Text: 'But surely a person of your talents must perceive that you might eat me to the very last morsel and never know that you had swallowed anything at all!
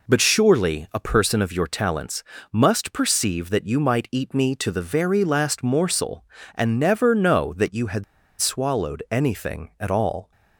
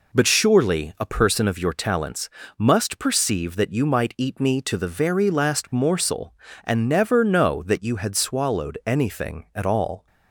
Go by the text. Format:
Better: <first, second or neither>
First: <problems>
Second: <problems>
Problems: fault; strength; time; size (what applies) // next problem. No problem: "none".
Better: second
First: pauses between "talents" and "must"; slight; at 2.2 s; 0.30 s long // pauses between "had" and "swallowed"; at 8.0 s; 0.36 s long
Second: pauses between "talents" and "must"; slight; at 2.2 s; 0.30 s long